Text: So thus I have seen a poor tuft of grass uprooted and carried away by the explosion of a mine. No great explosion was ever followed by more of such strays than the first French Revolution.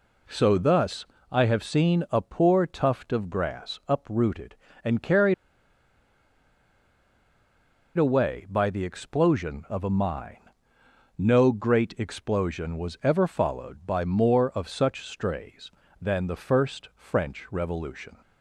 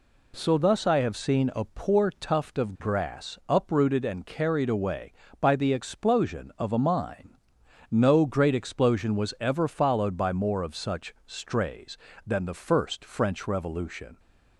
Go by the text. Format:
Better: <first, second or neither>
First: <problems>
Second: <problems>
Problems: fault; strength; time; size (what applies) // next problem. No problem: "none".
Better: second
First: pauses between "thus" and "I"; slight; at 1.0 s; 0.26 s long // pauses between "carried" and "away"; strong; at 5.3 s; 2.6 s long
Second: none